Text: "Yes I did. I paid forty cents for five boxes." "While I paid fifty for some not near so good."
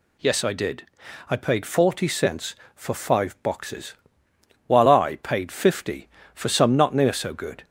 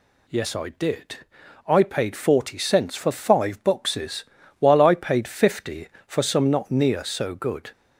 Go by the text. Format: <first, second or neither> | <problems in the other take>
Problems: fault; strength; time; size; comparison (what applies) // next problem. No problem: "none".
neither | none